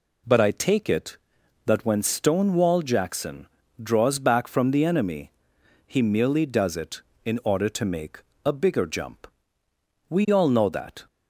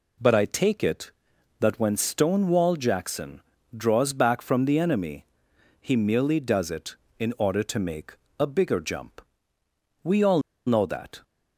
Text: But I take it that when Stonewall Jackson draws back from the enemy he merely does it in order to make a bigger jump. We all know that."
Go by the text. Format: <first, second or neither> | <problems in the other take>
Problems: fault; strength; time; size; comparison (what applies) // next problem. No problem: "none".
first | pauses between "Jackson" and "draws"; slight; at 3.4 s; 0.34 s long; slight in the first // pauses between "enemy" and "he"; noticeable; at 5.2 s; 0.56 s long; noticeable in the first // pauses between "make" and "a"; slight; at 8.1 s; 0.22 s long; slight in the first // pauses between "all" and "know"; slight; at 10.3 s; 0.26 s long